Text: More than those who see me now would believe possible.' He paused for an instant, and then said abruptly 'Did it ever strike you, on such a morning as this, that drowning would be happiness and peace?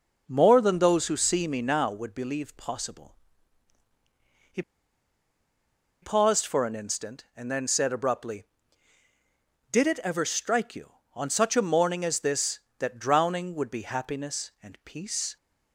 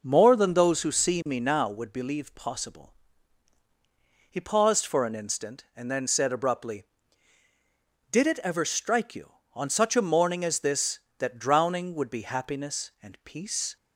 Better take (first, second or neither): second